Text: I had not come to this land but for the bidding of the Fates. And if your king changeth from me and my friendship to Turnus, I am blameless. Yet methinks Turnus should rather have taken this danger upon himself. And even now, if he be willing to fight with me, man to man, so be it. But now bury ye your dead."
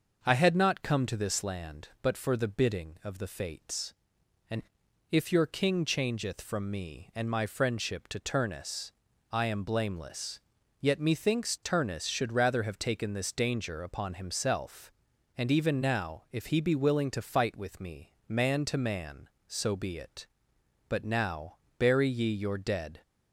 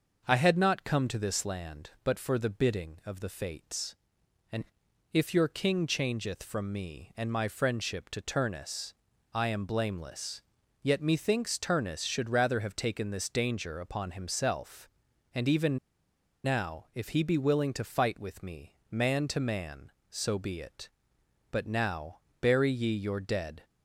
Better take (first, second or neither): first